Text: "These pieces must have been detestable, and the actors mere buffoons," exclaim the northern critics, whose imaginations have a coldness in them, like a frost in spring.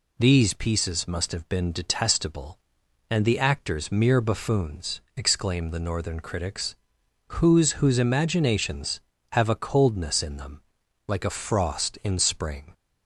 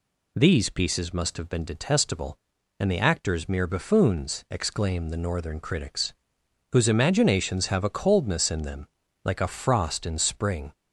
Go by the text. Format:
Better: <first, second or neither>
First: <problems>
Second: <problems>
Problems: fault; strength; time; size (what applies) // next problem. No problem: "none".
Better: second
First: says "whose" twice; at 7.7 s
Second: none